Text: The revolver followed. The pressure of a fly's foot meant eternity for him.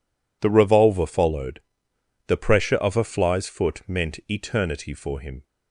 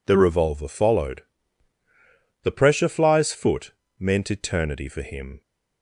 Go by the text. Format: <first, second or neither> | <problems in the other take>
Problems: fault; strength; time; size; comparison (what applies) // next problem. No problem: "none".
first | skips "of a"; at 2.8 s // pauses between "foot" and "meant"; slight; at 3.7 s; 0.26 s long